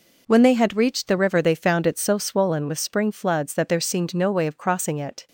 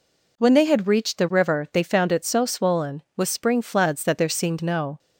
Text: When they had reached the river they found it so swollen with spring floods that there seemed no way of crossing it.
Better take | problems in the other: first | stops before "way of crossing it"; at 4.9 s

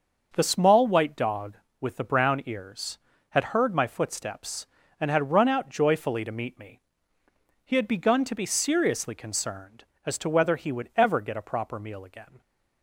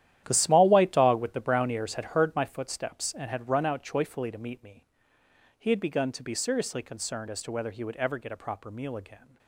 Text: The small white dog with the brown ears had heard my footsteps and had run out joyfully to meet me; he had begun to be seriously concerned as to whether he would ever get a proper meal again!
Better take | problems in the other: first | gets quieter; strong; throughout; 13.5 dB

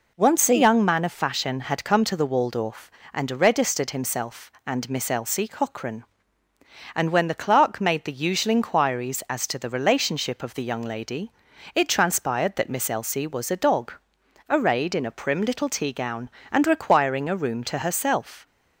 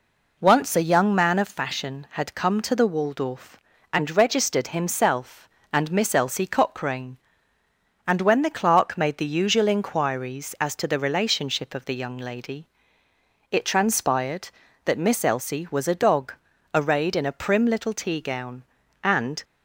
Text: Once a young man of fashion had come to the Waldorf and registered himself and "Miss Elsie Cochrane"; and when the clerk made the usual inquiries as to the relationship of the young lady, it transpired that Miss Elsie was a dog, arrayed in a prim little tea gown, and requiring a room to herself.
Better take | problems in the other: first | stops before "requiring a room to herself"; at 19.4 s

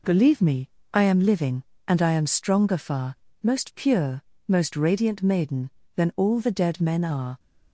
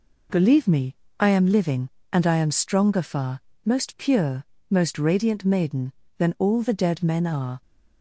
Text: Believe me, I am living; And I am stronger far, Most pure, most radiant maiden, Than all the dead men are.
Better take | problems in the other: neither | none

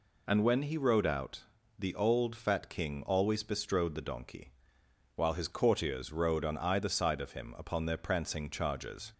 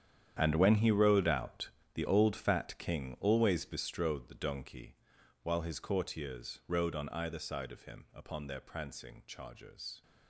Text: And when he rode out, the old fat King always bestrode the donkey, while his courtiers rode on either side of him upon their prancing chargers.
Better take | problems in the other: first | gets quieter; strong; throughout; 15 dB

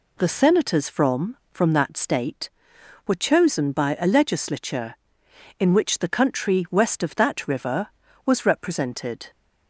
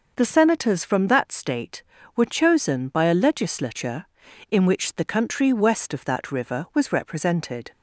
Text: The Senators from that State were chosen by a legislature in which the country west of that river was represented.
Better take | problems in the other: second | says "from" twice; at 1.5 s

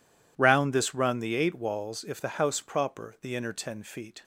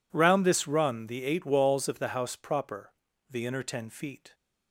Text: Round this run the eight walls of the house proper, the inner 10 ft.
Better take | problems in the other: second | says "if" for "of"; at 2.0 s

